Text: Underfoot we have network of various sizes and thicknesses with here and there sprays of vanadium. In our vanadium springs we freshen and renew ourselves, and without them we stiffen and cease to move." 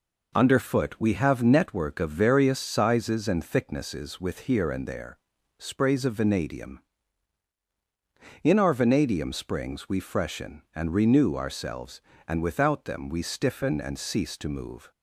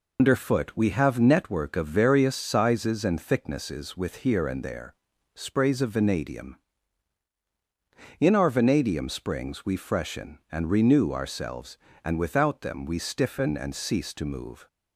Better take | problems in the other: first | loses the start of "Underfoot"; at 0.1 s; 85 ms // pauses between "there" and "sprays"; at 4.9 s; 0.40 s long; also in the first

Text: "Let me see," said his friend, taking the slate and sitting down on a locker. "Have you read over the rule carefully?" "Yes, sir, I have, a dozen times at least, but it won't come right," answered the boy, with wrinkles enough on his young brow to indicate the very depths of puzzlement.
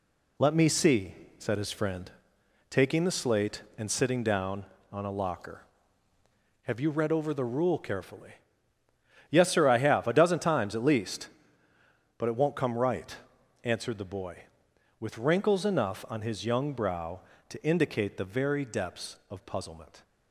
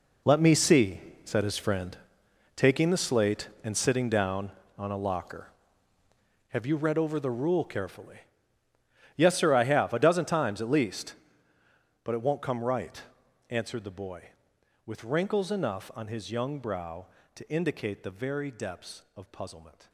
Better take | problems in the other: first | gets quieter; strong; throughout; 13 dB

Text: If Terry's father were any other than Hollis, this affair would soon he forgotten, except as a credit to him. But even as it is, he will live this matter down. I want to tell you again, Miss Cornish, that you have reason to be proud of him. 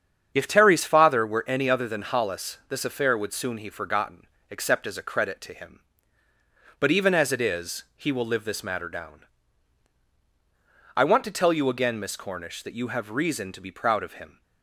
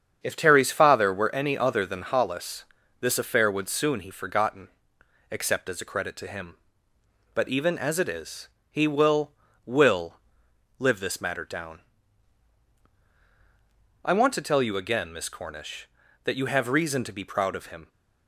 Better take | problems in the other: first | starts louder than the rest; strong; until 1.2 s; 7.5 dB; strong in the first // says "will" twice; at 9.6 s

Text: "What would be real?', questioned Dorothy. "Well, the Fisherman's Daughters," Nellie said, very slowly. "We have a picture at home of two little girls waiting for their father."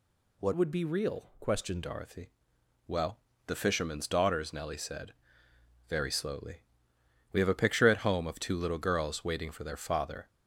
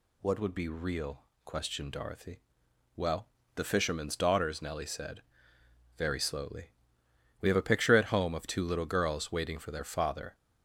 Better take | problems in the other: second | changes voice from "would" to "questioned"; from 0.5 to 1.8 s; 1.3 s long

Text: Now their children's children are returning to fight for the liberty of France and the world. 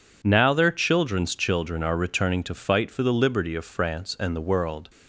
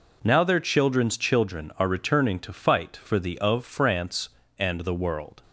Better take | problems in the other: first | skips "liberty"; at 3.3 s

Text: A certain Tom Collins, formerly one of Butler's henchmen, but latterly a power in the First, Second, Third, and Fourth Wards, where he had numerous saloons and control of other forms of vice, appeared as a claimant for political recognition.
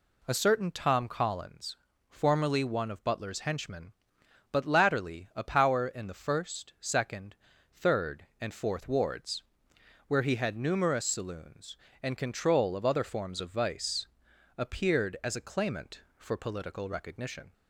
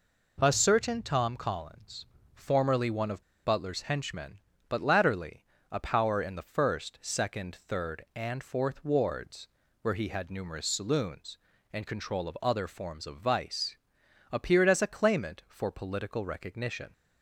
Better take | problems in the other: first | pauses between "of" and "Butler's"; slight; at 3.2 s; 0.22 s long // pauses between "latterly" and "a"; slight; at 5.4 s; 0.26 s long

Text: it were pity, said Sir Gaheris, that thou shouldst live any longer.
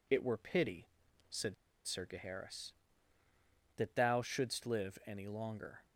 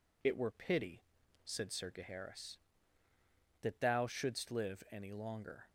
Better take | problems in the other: second | pauses between "said" and "Sir"; slight; at 1.5 s; 0.32 s long

